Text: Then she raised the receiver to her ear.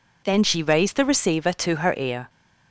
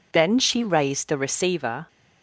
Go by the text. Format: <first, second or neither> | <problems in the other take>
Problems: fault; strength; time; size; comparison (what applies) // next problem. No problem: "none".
first | stops before "to her ear"; at 1.8 s